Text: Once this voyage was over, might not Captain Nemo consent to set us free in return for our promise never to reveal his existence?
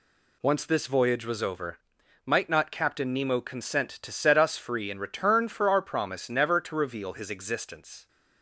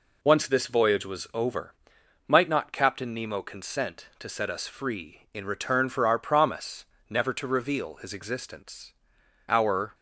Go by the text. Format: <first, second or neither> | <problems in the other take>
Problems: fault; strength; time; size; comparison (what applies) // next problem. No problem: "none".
first | pauses between "promise" and "never"; slight; at 6.8 s; 0.24 s long // goes on to say "Our"; slight; from 9.4 s on; 0.46 s long